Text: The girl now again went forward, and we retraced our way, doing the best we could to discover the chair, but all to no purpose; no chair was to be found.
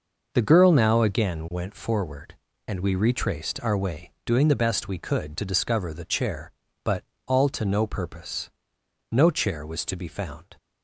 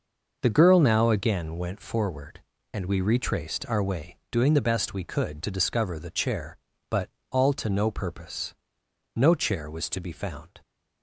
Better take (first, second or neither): neither